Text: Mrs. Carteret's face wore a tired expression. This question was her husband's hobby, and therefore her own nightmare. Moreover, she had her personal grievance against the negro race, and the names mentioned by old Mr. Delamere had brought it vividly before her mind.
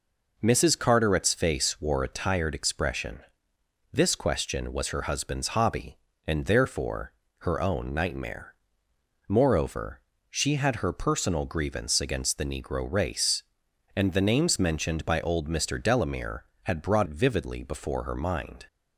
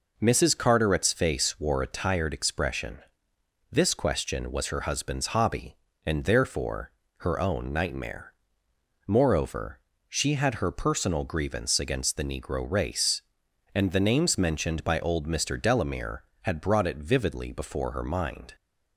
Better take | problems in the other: second | pauses between "therefore" and "her"; slight; at 7.1 s; 0.26 s long; slight in the second // skips "it"; at 17.0 s

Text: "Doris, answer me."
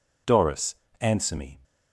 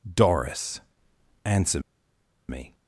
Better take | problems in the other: first | pauses between "answer" and "me"; noticeable; at 1.7 s; 0.70 s long

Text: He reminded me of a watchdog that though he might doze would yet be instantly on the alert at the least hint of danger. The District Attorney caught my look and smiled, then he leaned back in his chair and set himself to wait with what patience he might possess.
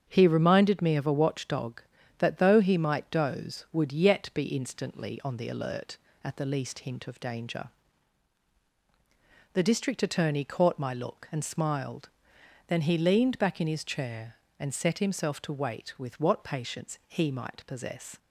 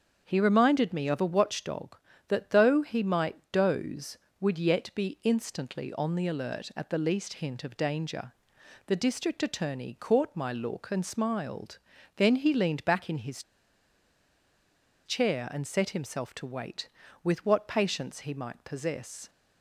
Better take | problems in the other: first | starts louder than the rest; strong; until 1.2 s; 7.5 dB; strong in the first // pauses between "his" and "chair"; strong; at 13.4 s; 1.6 s long

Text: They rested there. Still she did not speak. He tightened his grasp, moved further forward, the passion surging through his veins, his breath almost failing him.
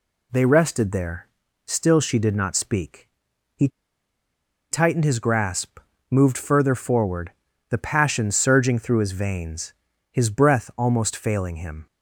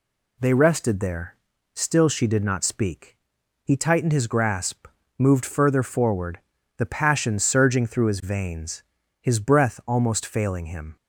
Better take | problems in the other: second | pauses between "He" and "tightened"; at 3.6 s; 1.0 s long

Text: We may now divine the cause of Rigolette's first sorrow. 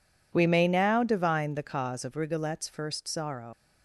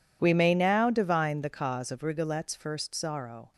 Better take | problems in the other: second | leaves "sorrow" unfinished; at 3.5 s; 120 ms

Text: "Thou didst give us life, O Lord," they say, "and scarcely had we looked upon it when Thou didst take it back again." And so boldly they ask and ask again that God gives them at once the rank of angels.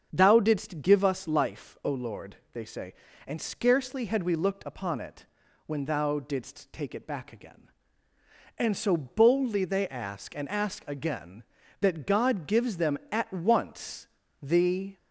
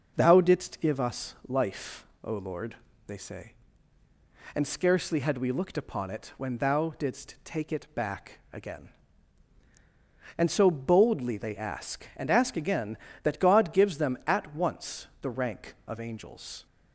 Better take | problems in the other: second | starts louder than the rest; strong; until 1.1 s; 7.5 dB // pauses between "it" and "when"; at 5.2 s; 0.42 s long // pauses between "once" and "the"; slight; at 14.0 s; 0.34 s long // stops before "rank of angels"; at 14.9 s

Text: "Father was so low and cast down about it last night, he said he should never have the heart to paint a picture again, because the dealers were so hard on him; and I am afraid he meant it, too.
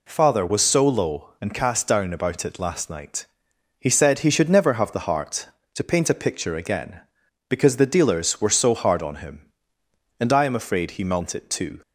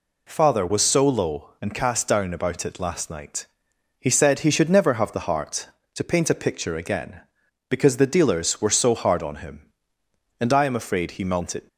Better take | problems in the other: first | stops before "too"; at 11.6 s

